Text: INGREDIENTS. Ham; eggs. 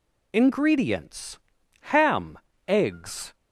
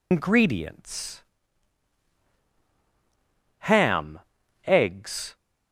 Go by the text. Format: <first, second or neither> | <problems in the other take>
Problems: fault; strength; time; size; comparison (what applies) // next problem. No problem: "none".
first | loses the start of "INGREDIENTS"; at 0.1 s; 165 ms